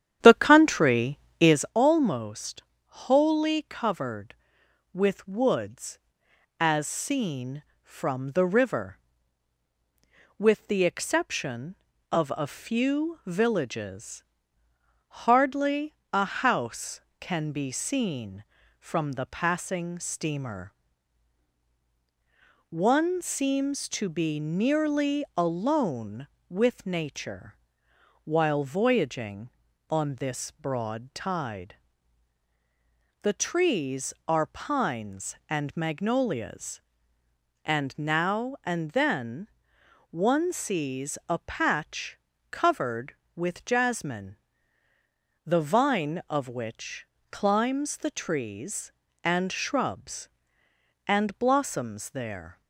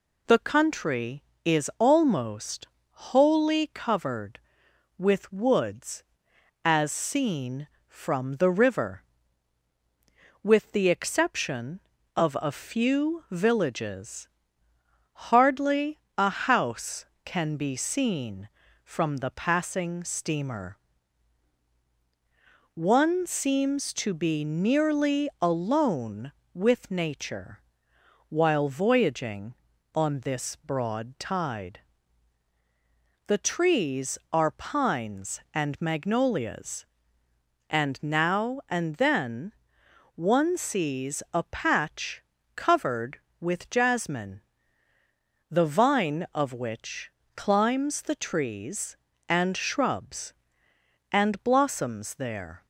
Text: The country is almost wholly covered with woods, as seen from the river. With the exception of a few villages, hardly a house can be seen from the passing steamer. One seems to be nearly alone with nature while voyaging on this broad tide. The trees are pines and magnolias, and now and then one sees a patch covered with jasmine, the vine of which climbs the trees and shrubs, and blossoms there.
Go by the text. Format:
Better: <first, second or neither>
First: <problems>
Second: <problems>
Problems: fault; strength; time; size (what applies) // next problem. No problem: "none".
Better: second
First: starts louder than the rest; strong; until 1.8 s; 10 dB // pauses between "almost" and "wholly"; slight; at 2.6 s; 0.24 s long // pauses between "hardly" and "a"; slight; at 15.9 s; 0.18 s long // pauses between "nature" and "while"; noticeable; at 27.5 s; 0.70 s long // pauses between "then" and "one"; noticeable; at 39.4 s; 0.62 s long // pauses between "patch" and "covered"; slight; at 42.1 s; 0.36 s long // pauses between "which" and "climbs"; slight; at 47.0 s; 0.28 s long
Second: pauses between "almost" and "wholly"; slight; at 2.6 s; 0.24 s long // pauses between "hardly" and "a"; slight; at 15.9 s; 0.18 s long // pauses between "nature" and "while"; noticeable; at 27.5 s; 0.70 s long // pauses between "then" and "one"; noticeable; at 39.5 s; 0.62 s long // pauses between "patch" and "covered"; slight; at 42.2 s; 0.36 s long // pauses between "which" and "climbs"; slight; at 47.0 s; 0.28 s long